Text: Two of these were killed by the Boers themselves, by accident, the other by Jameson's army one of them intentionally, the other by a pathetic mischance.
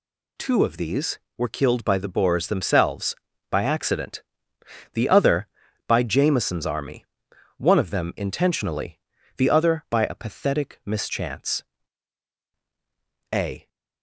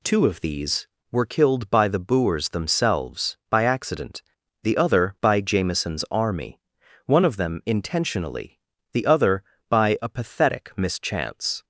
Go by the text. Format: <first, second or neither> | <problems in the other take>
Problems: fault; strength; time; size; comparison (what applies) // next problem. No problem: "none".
second | pauses between "army" and "one"; noticeable; at 7.0 s; 0.52 s long; noticeable in the second // goes on to say "A"; slight; from 13.3 s on; 0.36 s long